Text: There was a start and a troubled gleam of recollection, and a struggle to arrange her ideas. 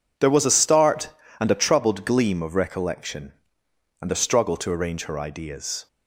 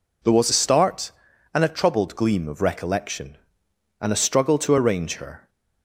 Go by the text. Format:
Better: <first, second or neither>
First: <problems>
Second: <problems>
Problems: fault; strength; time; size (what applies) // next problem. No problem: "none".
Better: first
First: none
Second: stops before "ideas"; at 5.4 s